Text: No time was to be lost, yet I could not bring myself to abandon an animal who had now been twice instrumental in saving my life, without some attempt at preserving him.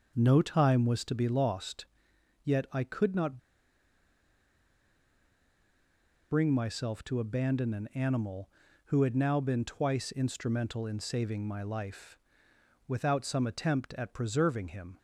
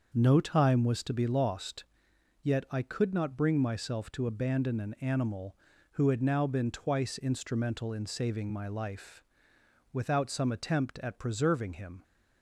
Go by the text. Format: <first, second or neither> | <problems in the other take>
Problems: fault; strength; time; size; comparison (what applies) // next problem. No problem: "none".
second | starts louder than the rest; until 1.1 s; 6.5 dB; also in the second // pauses between "not" and "bring"; strong; at 3.3 s; 2.9 s long